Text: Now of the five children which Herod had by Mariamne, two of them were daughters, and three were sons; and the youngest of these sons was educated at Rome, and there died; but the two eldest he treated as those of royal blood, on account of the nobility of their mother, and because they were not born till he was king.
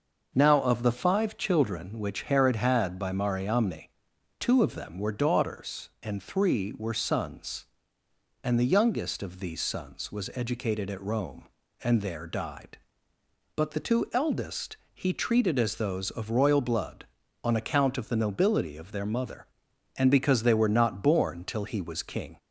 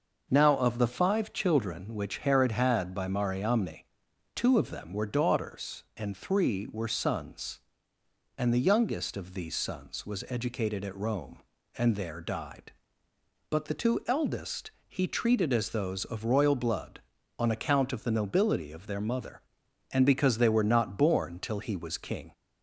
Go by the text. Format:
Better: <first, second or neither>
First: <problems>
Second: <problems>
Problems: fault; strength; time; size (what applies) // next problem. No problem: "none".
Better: neither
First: pauses between "eldest" and "he"; slight; at 14.7 s; 0.18 s long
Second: pauses between "eldest" and "he"; slight; at 14.7 s; 0.18 s long